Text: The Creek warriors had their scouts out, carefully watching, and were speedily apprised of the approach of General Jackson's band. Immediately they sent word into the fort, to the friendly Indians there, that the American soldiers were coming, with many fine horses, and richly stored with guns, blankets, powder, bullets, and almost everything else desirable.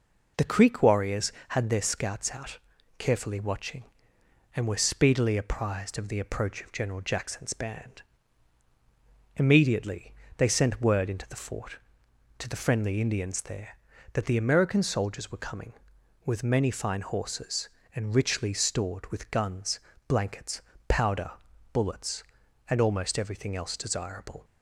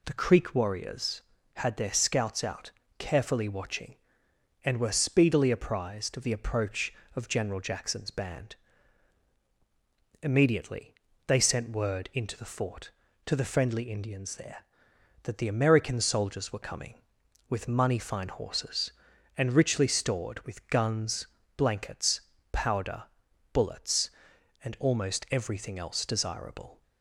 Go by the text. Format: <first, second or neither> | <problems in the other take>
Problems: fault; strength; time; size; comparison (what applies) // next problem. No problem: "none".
first | pauses between "Immediately" and "they"; slight; at 10.9 s; 0.32 s long; slight in the first // says "money" for "many"; at 17.6 s